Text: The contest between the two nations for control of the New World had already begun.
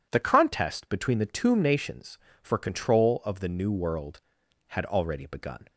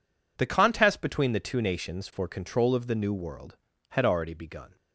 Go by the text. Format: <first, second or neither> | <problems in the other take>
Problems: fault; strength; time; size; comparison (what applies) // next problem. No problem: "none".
second | says "tomb" for "two"; at 1.2 s